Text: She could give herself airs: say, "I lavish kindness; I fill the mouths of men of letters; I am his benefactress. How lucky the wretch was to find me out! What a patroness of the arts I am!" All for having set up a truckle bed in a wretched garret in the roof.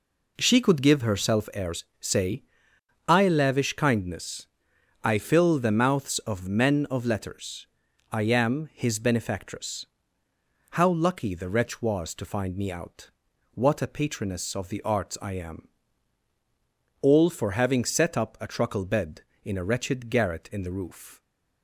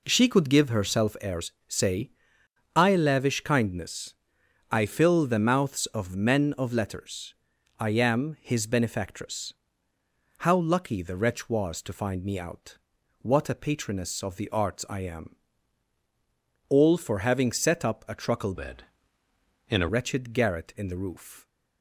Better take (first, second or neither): first